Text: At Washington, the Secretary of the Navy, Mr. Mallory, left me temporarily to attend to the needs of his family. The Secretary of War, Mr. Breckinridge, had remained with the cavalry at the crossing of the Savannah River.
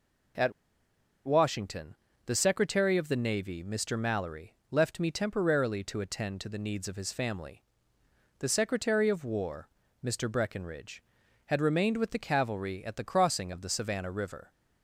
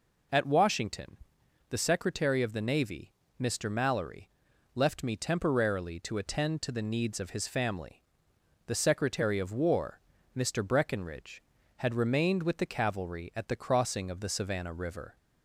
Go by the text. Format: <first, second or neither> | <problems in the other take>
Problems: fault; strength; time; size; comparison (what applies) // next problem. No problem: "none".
second | pauses between "At" and "Washington"; noticeable; at 0.5 s; 0.73 s long